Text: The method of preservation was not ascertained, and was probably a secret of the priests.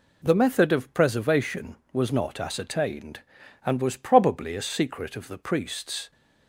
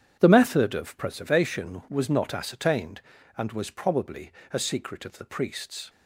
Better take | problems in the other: first | starts louder than the rest; strong; until 1.2 s; 9 dB // pauses between "probably" and "a"; slight; at 4.3 s; 0.20 s long

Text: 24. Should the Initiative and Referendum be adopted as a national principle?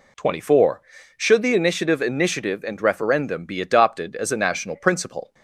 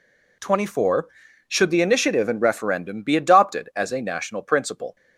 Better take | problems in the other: second | says "Initiative" twice; at 1.9 s

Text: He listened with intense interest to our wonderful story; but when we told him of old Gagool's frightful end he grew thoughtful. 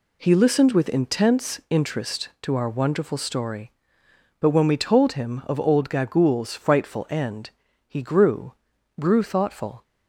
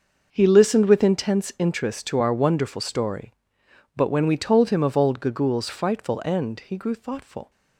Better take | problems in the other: second | pauses between "end" and "he"; slight; at 7.5 s; 0.36 s long // says "grew" twice; at 8.9 s

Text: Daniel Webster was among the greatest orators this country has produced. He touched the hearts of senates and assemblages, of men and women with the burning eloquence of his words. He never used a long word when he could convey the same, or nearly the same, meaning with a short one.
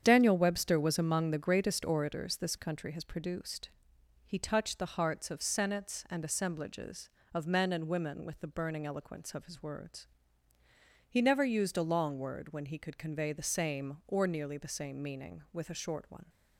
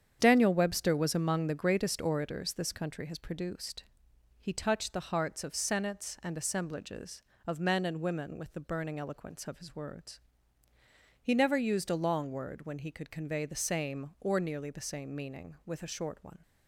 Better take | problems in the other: neither | starts louder than the rest; strong; the same in both

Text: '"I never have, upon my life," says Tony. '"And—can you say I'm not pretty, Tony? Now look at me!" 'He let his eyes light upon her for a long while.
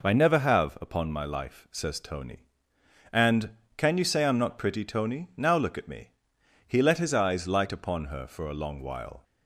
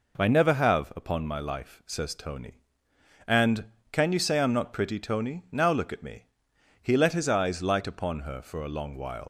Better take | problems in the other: first | leaves "while" unfinished; at 9.2 s; 100 ms

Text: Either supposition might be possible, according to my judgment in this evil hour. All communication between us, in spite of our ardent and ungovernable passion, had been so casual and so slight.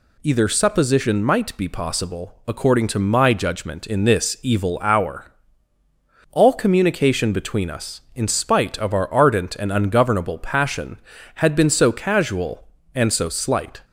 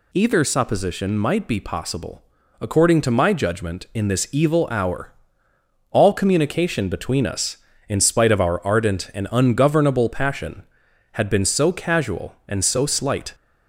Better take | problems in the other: neither | none

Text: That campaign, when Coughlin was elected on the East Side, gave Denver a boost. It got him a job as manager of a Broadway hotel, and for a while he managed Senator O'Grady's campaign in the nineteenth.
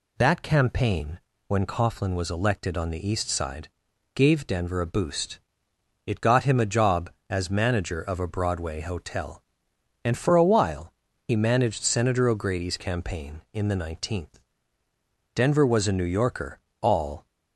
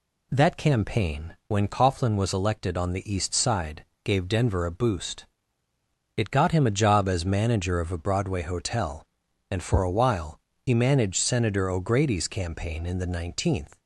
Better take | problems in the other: second | pauses between "while" and "he"; slight; at 10.9 s; 0.36 s long; slight in the second // goes on to say "Denver was a New Yorker all"; strong; from 15.3 s on; 1.9 s long

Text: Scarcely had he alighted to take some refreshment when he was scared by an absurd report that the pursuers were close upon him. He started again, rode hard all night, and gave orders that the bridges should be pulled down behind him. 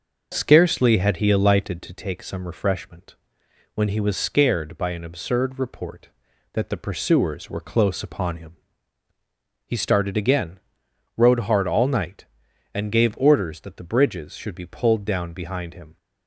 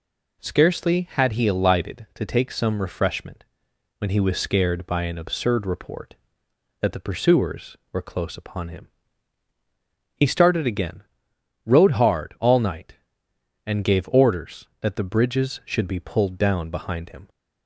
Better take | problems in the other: second | starts louder than the rest; noticeable; until 1.8 s; 6 dB // pauses between "refreshment" and "when"; noticeable; at 3.1 s; 0.58 s long; noticeable in the second

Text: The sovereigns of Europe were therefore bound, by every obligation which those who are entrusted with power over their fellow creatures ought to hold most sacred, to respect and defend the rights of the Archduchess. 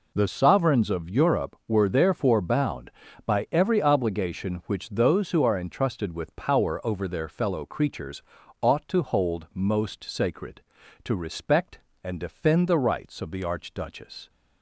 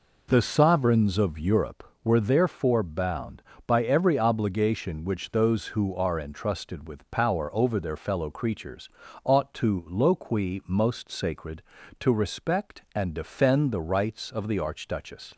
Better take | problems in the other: first | pauses between "creatures" and "ought"; slight; at 8.8 s; 0.34 s long; also in the first // says "loqui" for "hold"; at 9.8 s

